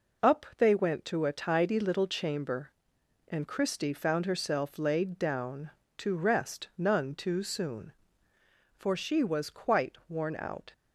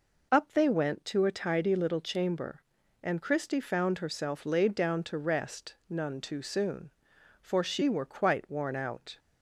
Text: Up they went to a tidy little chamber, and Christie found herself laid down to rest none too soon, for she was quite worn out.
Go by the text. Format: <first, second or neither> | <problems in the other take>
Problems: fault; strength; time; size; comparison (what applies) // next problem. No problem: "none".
first | says "were" for "was"; at 7.8 s